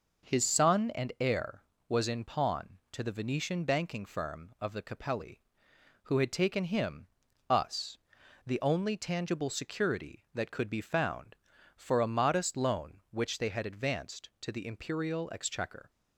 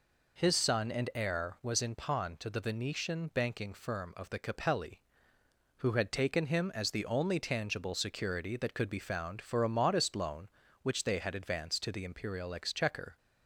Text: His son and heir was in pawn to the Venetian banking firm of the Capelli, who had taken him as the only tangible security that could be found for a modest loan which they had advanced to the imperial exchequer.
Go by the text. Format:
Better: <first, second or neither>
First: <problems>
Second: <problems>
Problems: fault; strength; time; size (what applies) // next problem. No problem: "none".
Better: second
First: says "us" for "as"; at 7.4 s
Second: none